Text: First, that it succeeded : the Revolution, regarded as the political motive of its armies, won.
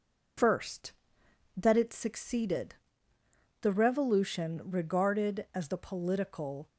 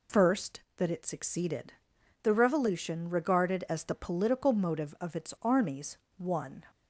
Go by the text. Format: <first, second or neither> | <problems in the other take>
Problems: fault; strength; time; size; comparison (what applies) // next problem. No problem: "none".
second | stops before "motive of its armies won"; at 6.6 s